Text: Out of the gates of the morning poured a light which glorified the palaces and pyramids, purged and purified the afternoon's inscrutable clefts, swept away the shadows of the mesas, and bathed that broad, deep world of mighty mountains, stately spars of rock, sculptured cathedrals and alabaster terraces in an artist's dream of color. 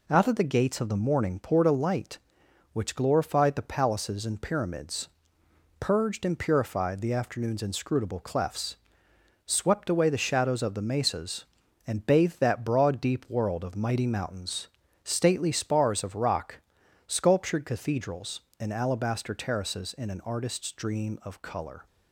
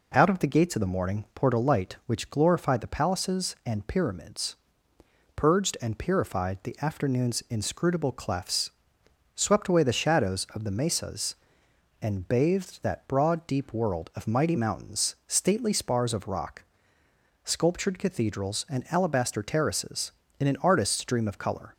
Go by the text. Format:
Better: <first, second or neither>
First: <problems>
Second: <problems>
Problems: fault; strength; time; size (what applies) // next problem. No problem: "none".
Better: neither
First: none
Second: none